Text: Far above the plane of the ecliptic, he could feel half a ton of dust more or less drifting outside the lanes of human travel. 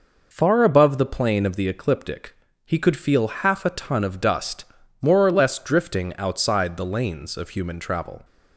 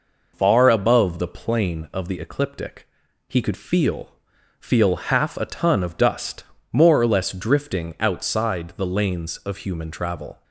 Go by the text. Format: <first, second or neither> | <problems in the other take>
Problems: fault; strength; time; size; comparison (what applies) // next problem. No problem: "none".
first | says "feel" twice; at 4.5 s // pauses between "dust" and "more"; slight; at 6.4 s; 0.28 s long; also in the first